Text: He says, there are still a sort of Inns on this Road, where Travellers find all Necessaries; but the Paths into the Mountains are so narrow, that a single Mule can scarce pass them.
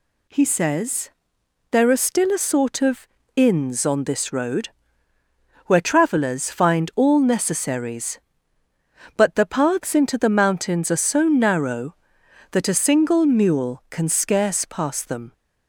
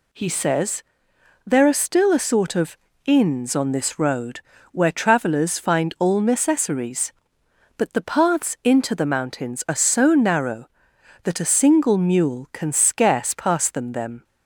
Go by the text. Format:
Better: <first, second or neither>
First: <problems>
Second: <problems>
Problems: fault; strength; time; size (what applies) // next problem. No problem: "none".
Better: first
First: pauses between "of" and "Inns"; slight; at 3.0 s; 0.26 s long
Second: pauses between "of" and "Inns"; slight; at 2.7 s; 0.28 s long // says "them" twice; at 13.9 s